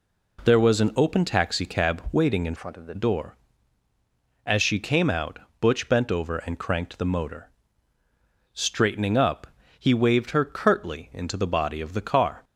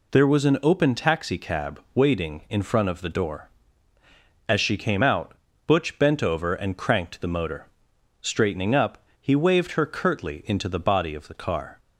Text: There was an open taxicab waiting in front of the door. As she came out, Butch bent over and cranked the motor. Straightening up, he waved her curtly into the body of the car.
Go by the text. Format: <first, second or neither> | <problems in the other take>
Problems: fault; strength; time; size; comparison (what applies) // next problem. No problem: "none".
second | changes voice from "front" to "the"; from 2.5 to 2.9 s; 0.4 s long